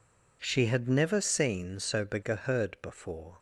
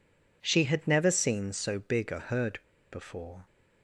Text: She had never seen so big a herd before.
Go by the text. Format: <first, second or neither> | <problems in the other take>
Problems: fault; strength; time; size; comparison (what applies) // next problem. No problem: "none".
first | pauses between "herd" and "before"; slight; at 2.5 s; 0.32 s long